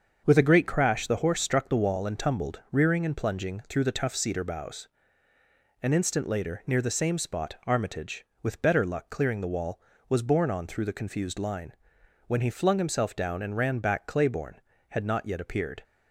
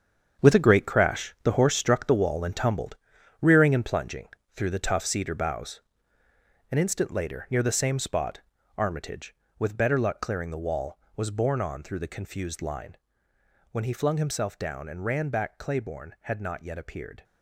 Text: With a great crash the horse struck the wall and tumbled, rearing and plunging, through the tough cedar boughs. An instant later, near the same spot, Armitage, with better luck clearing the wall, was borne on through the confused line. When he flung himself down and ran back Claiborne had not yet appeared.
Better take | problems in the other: first | gets quieter; strong; throughout; 11 dB // starts louder than the rest; strong; until 1.4 s; 7.5 dB; also in the first

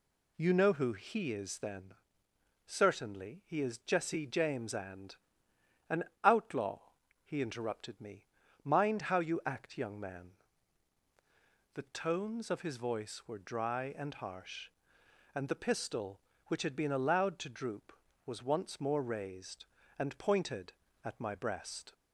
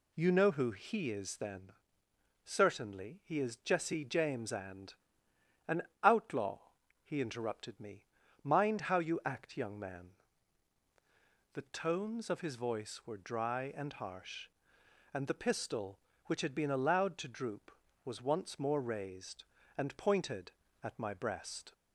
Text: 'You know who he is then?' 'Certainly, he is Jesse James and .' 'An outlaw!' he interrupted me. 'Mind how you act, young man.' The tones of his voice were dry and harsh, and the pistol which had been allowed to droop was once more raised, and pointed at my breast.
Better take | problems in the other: neither | pauses between "An" and "outlaw"; slight; the same in both

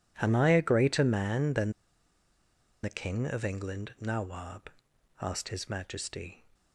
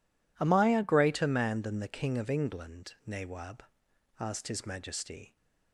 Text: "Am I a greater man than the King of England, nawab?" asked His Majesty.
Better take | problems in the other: second | pauses between "than" and "the"; at 1.7 s; 1.1 s long

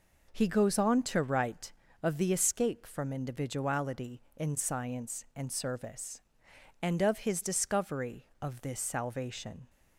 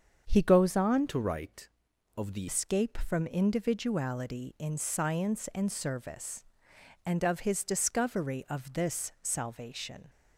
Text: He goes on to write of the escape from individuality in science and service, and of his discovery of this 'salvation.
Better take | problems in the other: first | starts louder than the rest; until 1.2 s; 7 dB // changes voice from "to" to "the"; from 1.0 to 2.4 s; 1.4 s long

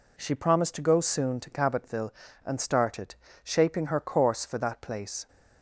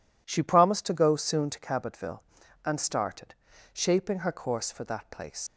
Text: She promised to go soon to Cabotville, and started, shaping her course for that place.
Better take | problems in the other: first | leaves "place" unfinished; at 5.4 s; 115 ms

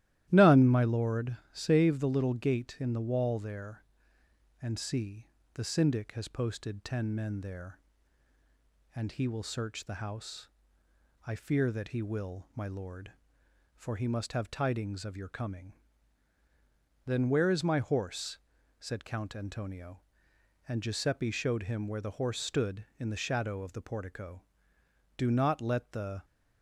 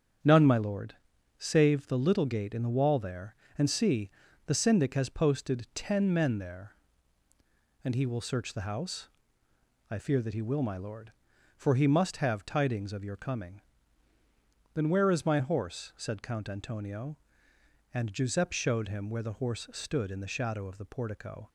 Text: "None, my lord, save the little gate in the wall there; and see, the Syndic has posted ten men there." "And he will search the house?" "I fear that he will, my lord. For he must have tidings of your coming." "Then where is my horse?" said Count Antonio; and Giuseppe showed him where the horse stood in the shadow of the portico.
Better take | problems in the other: second | starts louder than the rest; strong; until 1.3 s; 14 dB; strong in the second // goes on to say "Do not let the"; noticeable; from 25.1 s on; 1.0 s long

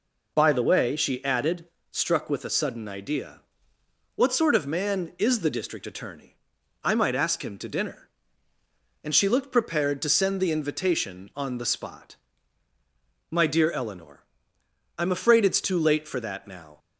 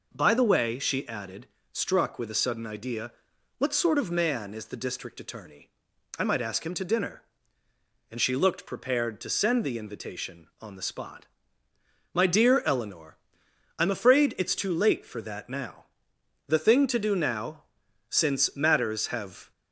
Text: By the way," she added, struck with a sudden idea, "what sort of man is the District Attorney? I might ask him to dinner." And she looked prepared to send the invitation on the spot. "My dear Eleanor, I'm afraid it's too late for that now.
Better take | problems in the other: first | goes on to say "The thing to do now since matters have"; strong; from 16.4 s on; 3.0 s long

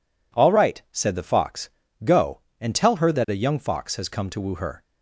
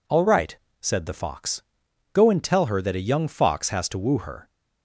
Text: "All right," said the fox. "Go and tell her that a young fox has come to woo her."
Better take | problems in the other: first | skips "come"; at 3.8 s

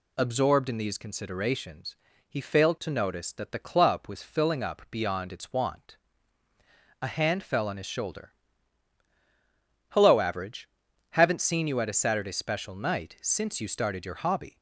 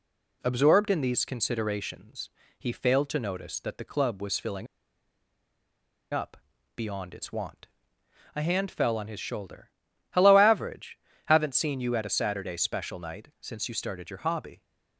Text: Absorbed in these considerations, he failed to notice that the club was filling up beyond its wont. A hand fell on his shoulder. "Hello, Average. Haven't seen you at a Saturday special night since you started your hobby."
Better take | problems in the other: first | pauses between "filling" and "up"; strong; at 4.6 s; 1.4 s long // pauses between "up" and "beyond"; at 6.3 s; 0.38 s long

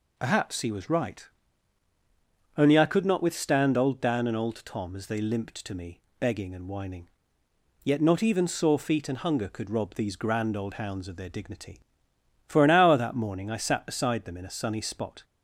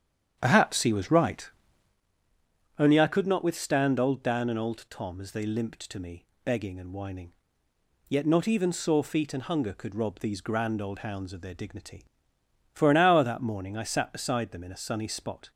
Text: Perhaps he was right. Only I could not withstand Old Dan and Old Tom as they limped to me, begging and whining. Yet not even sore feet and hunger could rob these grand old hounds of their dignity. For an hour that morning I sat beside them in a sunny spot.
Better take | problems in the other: first | starts louder than the rest; strong; until 2.0 s; 9 dB

